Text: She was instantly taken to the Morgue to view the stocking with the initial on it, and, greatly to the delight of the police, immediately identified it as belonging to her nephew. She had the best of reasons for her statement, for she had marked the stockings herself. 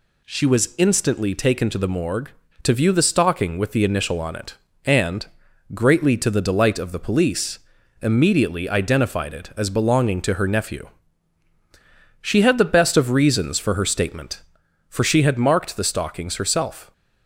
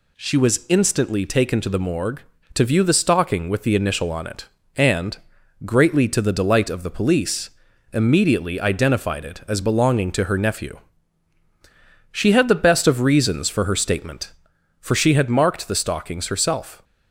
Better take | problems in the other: neither | none

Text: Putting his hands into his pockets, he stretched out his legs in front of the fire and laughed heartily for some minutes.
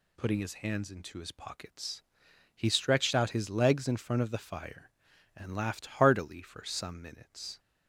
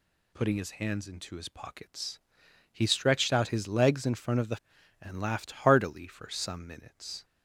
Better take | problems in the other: first | skips "fire"; at 4.7 s

